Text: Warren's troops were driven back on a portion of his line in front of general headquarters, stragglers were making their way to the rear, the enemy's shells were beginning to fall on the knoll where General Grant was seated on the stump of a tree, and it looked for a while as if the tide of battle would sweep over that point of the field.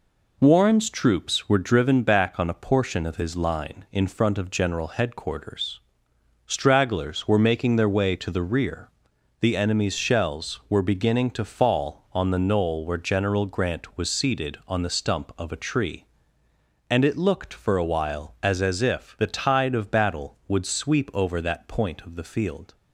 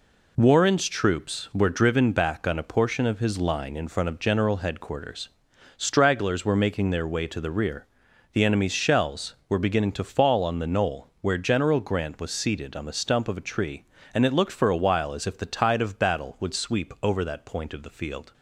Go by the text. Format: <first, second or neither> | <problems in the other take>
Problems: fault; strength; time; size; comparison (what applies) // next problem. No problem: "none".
second | says "as" twice; at 18.6 s